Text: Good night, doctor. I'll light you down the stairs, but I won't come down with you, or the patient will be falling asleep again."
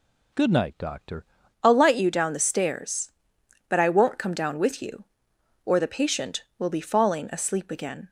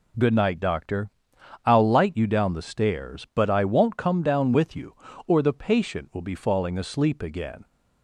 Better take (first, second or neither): second